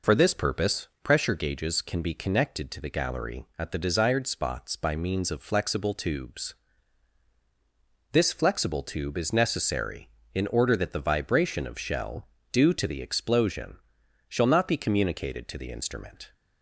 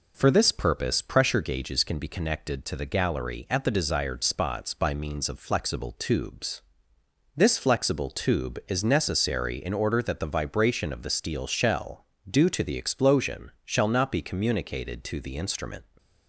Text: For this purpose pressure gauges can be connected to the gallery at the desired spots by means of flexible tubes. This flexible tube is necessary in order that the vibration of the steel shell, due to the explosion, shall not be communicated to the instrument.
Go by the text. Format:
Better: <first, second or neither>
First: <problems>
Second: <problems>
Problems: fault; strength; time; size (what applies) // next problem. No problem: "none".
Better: second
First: pauses between "purpose" and "pressure"; slight; at 0.8 s; 0.16 s long // skips "the steel"; at 11.7 s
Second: none